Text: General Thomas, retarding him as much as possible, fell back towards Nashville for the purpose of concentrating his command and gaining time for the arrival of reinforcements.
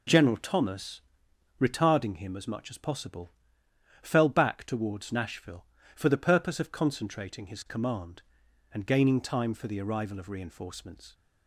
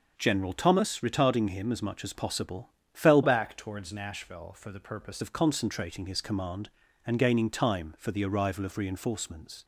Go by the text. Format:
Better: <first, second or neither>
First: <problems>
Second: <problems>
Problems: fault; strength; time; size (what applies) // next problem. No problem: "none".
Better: first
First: none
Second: changes voice from "back" to "purpose"; from 3.2 to 5.2 s; 2.0 s long